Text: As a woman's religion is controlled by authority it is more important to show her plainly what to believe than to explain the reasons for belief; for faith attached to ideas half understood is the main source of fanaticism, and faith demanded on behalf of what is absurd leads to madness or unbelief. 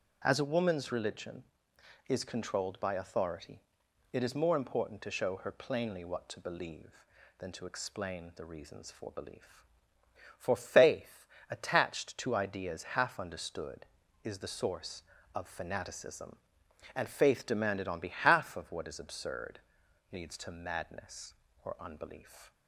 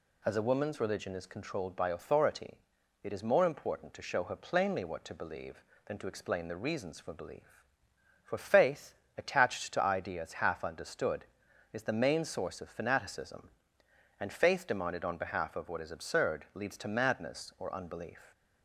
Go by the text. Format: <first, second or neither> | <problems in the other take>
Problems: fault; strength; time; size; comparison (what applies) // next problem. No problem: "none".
second | starts louder than the rest; until 1.2 s; 6.5 dB // pauses between "authority" and "it"; noticeable; at 3.6 s; 0.52 s long; noticeable in the second // pauses between "faith" and "attached"; slight; at 11.2 s; 0.24 s long; slight in the second // skips "main"; at 14.5 s // pauses between "absurd" and "leads"; noticeable; at 19.5 s; 0.54 s long